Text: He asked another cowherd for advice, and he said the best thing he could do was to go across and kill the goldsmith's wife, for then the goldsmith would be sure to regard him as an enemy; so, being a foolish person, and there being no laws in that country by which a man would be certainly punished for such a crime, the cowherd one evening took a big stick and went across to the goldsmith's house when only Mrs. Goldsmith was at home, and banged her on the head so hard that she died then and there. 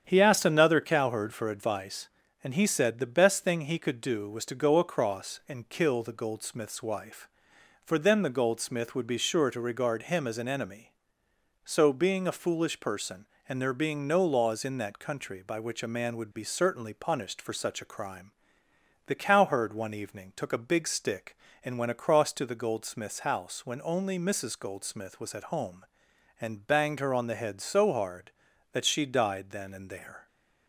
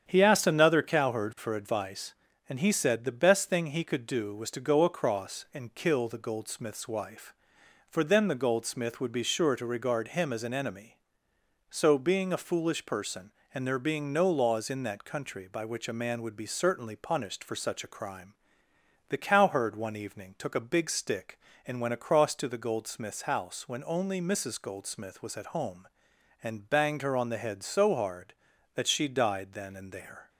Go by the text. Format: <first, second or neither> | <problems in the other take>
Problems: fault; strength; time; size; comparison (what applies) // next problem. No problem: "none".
neither | starts louder than the rest; strong; the same in both